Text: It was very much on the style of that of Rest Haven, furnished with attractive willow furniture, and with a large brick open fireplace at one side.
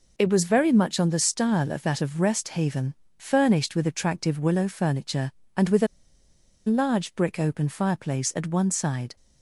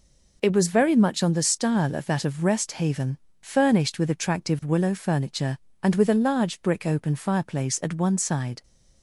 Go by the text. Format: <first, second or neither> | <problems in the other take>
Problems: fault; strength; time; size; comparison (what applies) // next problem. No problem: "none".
second | pauses between "a" and "large"; noticeable; at 5.8 s; 0.80 s long